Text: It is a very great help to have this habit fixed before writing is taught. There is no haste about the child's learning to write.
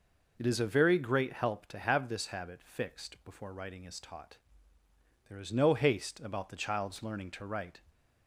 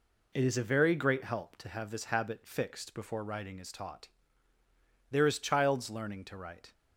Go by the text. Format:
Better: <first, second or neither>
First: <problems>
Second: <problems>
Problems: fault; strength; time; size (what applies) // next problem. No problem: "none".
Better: first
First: none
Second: skips "no haste about the"; at 5.3 s